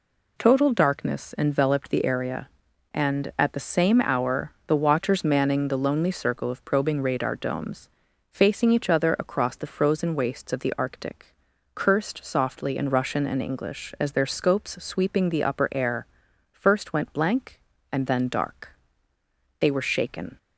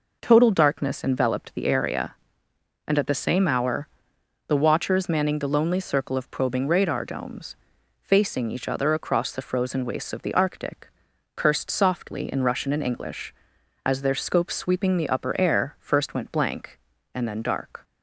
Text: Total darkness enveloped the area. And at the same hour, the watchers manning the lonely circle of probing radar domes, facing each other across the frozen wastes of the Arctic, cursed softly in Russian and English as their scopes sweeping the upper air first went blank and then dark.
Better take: second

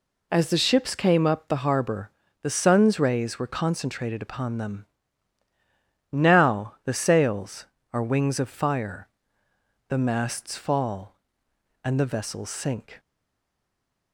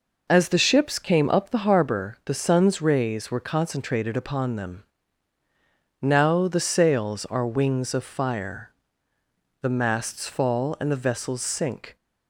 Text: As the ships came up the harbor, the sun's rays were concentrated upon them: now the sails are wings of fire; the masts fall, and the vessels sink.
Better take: second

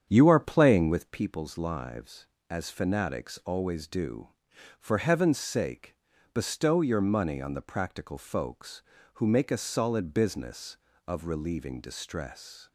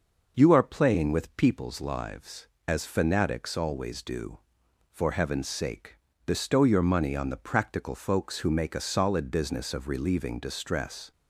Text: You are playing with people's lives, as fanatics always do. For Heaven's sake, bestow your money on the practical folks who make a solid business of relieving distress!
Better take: second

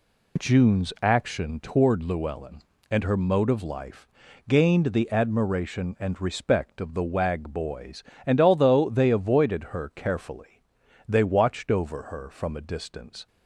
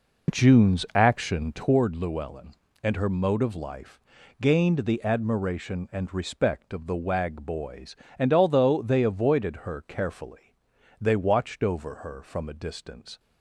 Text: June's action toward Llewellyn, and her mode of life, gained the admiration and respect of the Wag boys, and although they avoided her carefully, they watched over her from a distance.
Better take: first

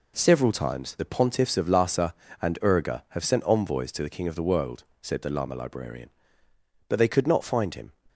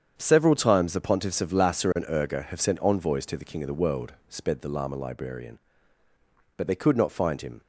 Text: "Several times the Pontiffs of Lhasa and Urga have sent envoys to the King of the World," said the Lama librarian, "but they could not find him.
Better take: first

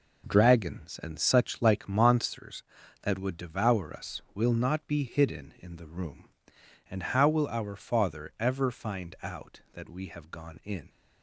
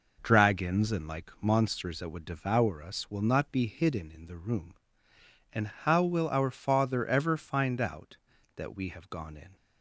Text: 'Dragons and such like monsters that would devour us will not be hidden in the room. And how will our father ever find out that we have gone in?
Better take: first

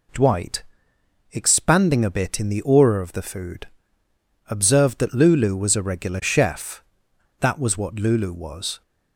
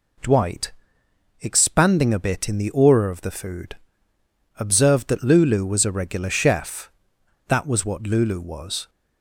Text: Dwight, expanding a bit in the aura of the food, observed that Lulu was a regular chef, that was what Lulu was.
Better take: neither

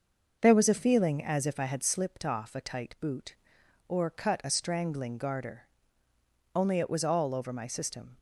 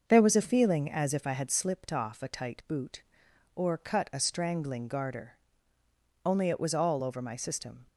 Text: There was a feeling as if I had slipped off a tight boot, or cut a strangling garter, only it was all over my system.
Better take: neither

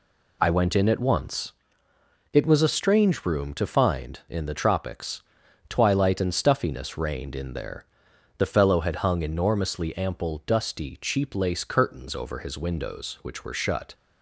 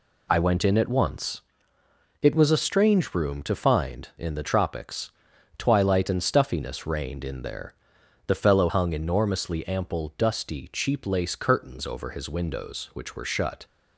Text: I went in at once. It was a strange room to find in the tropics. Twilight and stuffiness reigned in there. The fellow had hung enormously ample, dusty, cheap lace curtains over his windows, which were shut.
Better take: first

